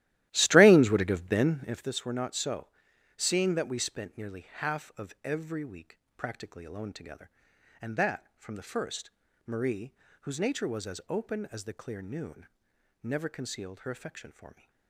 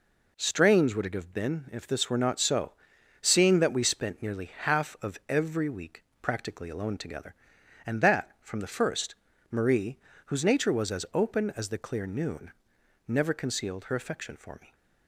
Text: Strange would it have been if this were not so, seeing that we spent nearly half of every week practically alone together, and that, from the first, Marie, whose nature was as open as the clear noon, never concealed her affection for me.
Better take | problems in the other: second | starts louder than the rest; strong; until 1.9 s; 14.5 dB // pauses between "week" and "practically"; slight; at 5.9 s; 0.20 s long; slight in the second

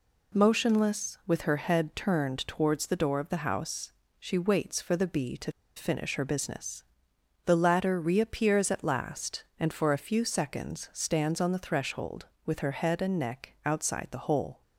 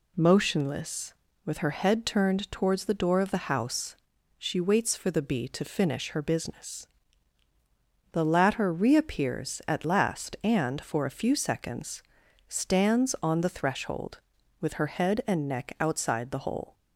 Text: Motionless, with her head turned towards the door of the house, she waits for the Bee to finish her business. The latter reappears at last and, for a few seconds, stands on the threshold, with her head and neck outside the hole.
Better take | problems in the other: second | pauses between "to" and "finish"; slight; at 5.5 s; 0.25 s long

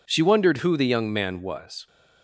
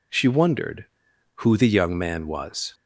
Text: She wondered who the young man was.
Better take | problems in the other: neither | none

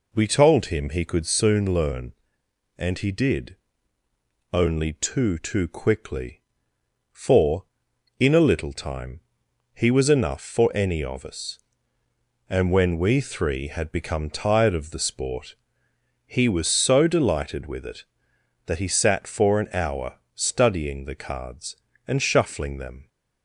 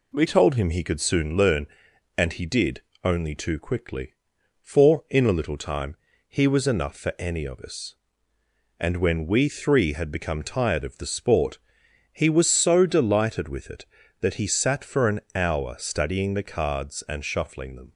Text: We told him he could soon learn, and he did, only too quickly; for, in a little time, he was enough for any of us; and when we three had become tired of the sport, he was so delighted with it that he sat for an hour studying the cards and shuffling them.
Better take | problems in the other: second | says "too" twice; at 5.3 s // pauses between "hour" and "studying"; slight; at 20.1 s; 0.18 s long

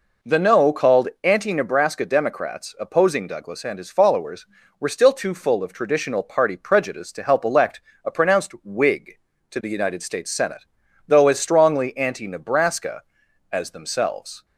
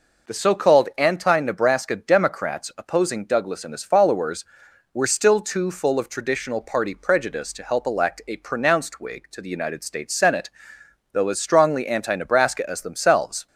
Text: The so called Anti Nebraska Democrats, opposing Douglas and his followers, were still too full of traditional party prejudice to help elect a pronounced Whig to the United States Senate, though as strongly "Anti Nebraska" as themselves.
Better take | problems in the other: second | says "no" for "so"; at 0.3 s // pauses between "called" and "Anti"; slight; at 1.0 s; 0.16 s long // pauses between "elect" and "a"; slight; at 7.8 s; 0.24 s long

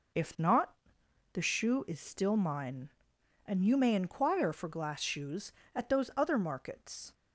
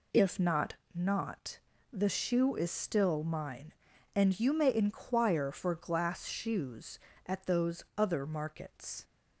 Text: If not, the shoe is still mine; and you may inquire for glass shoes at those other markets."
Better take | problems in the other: first | says "not" twice; at 0.9 s

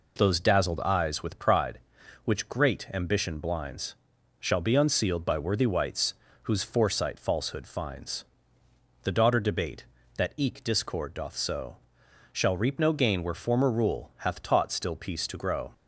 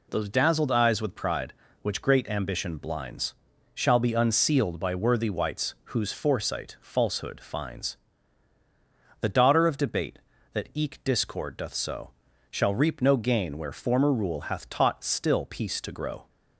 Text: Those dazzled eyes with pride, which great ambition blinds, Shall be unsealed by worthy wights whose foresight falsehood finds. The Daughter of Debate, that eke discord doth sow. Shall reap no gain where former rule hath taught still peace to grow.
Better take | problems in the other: second | pauses between "wights" and "whose"; slight; at 6.1 s; 0.30 s long // skips "of"; at 9.3 s

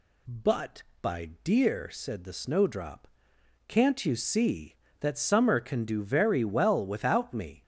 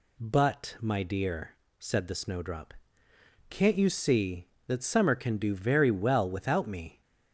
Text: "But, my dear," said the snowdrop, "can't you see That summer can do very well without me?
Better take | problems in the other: second | says "by" for "my"; at 1.0 s

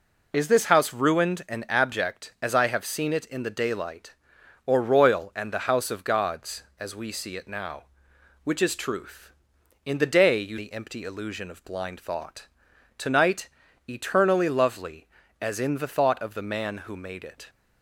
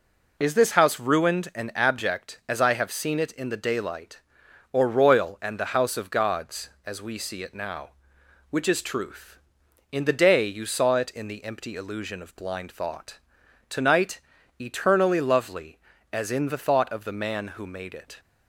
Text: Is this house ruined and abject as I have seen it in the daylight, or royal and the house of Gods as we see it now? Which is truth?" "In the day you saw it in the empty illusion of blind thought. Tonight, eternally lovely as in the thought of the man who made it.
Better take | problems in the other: second | skips "saw it in"; at 10.5 s

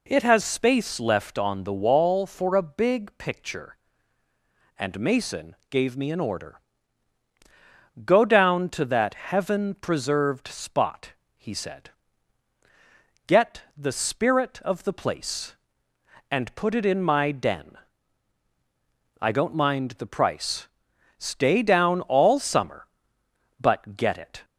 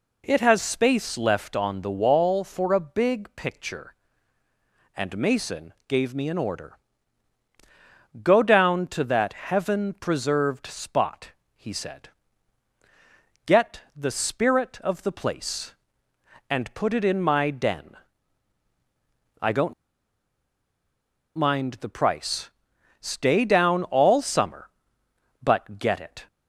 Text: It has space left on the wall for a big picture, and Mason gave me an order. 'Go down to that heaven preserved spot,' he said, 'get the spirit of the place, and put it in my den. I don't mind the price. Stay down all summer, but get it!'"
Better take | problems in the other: first | pauses between "don't" and "mind"; strong; at 19.7 s; 1.6 s long

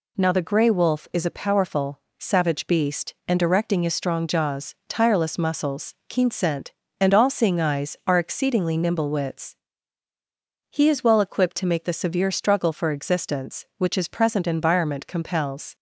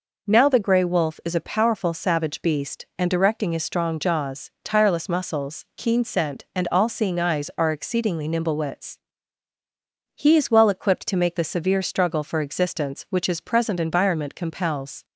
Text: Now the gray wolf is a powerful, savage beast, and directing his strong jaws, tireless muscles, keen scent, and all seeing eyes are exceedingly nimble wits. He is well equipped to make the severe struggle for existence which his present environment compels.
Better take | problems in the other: neither | none

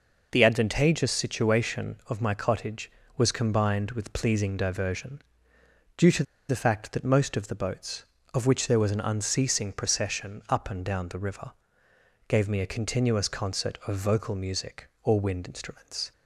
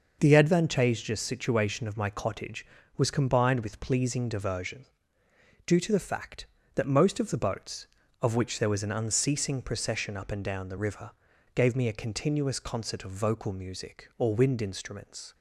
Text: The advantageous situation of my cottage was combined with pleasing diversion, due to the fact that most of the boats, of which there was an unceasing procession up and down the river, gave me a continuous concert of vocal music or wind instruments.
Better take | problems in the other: second | pauses between "to" and "the"; slight; at 6.2 s; 0.25 s long

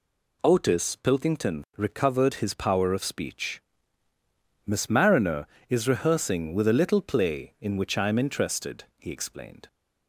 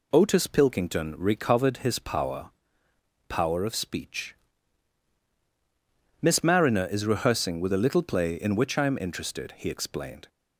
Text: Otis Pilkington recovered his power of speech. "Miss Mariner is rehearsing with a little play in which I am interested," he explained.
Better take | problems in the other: first | says "power" twice; at 3.2 s

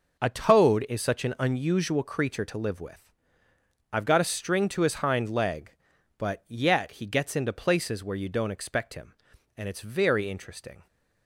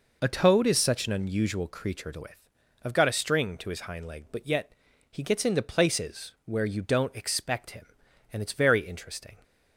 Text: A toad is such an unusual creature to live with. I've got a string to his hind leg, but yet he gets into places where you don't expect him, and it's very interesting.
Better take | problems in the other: first | skips "live"; at 2.2 s // pauses between "yet" and "he"; at 4.7 s; 0.38 s long

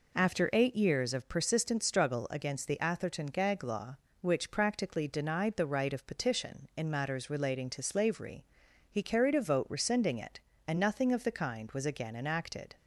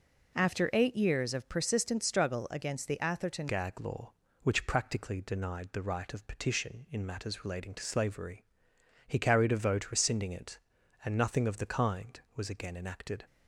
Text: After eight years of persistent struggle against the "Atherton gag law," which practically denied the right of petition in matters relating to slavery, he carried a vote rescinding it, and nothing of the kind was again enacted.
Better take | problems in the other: first | changes voice at "gag"; from 3.4 s on; 9.8 s long

